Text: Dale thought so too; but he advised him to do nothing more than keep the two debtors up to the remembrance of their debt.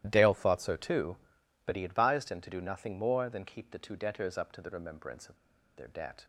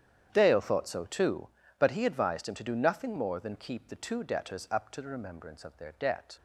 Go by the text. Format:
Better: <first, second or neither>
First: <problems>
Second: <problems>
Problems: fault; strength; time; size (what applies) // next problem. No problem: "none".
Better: second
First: starts louder than the rest; strong; until 1.0 s; 13 dB // pauses between "of" and "their"; at 5.3 s; 0.39 s long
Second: starts louder than the rest; strong; until 1.3 s; 9.5 dB